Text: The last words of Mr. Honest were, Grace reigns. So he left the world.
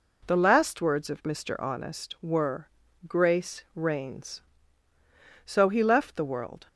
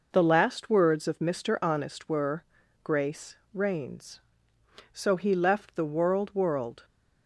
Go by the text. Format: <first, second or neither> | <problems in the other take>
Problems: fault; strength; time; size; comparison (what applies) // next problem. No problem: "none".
first | pauses between "Grace" and "reigns"; slight; at 3.3 s; 0.16 s long // says "world" twice; at 6.3 s